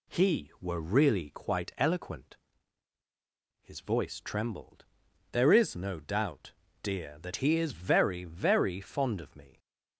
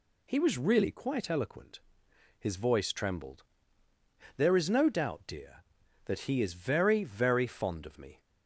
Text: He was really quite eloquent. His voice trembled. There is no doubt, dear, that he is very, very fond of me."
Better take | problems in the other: second | says "were" for "was"; at 0.6 s

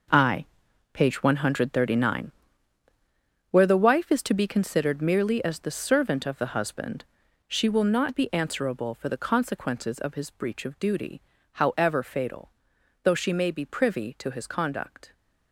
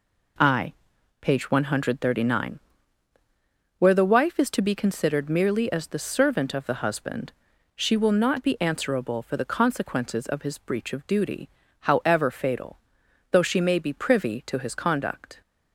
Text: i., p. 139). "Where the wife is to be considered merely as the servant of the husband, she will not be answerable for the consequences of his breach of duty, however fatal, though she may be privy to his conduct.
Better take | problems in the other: second | gets quieter; strong; throughout; 12.5 dB

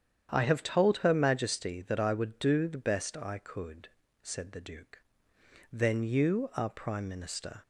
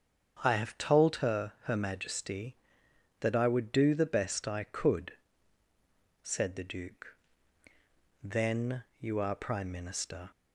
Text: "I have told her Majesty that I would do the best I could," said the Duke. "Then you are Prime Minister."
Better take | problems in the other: first | starts louder than the rest; strong; until 1.4 s; 7.5 dB; strong in the first // says "her" twice; at 1.6 s // pauses between "Then" and "you"; slight; at 8.8 s; 0.16 s long

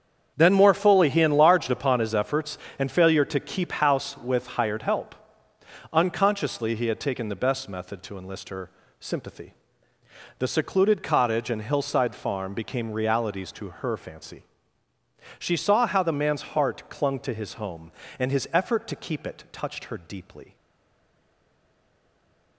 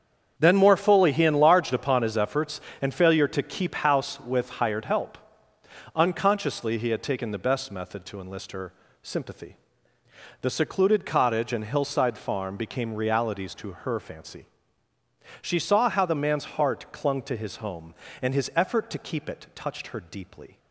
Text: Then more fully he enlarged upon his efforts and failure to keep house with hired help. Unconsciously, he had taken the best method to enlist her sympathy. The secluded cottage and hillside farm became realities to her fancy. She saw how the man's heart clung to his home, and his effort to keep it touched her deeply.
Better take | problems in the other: second | starts louder than the rest; strong; until 1.3 s; 7.5 dB; strong in the second // pauses between "her" and "sympathy"; slight; at 8.6 s; 0.30 s long; slight in the second // stays silent after the last word; noticeable; from 20.5 s on; 2.0 s long

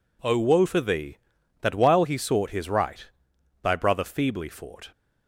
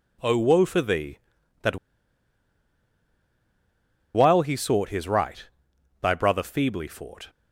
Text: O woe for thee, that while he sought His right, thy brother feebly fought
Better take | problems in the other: first | pauses between "that" and "while"; strong; at 1.7 s; 2.3 s long

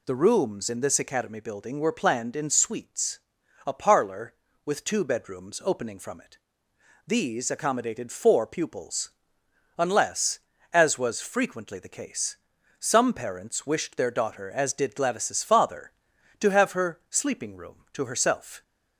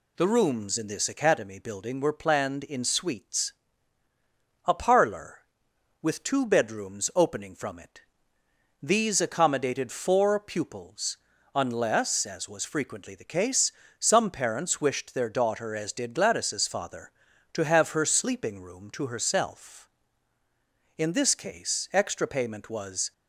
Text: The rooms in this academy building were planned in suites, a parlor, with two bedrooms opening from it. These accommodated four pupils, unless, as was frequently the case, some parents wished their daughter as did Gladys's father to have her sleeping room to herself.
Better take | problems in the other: first | goes on to say "In this case extra payment was"; strong; from 20.9 s on; 2.1 s long

